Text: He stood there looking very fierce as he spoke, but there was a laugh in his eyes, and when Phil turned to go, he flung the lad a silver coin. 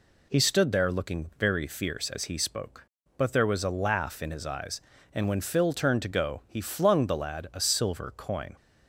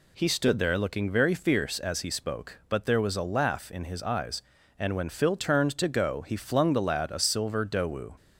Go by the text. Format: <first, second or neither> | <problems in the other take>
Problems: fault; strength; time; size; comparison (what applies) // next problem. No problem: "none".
first | says "dowu" for "coin"; at 7.6 s